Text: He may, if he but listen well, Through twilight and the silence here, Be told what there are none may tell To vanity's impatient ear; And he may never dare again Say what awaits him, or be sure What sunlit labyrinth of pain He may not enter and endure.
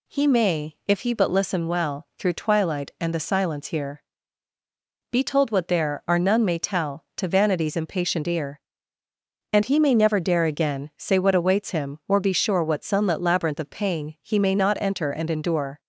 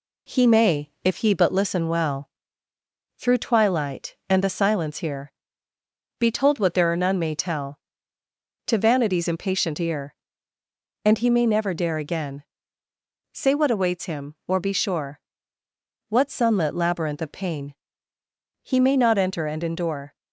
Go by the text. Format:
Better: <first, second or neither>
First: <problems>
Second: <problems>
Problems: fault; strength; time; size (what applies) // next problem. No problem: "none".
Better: first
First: none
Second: gets quieter; slight; throughout; 2.5 dB // pauses between "again" and "Say"; noticeable; at 12.4 s; 0.90 s long // pauses between "sure" and "What"; noticeable; at 15.2 s; 0.88 s long // pauses between "pain" and "He"; noticeable; at 17.7 s; 0.86 s long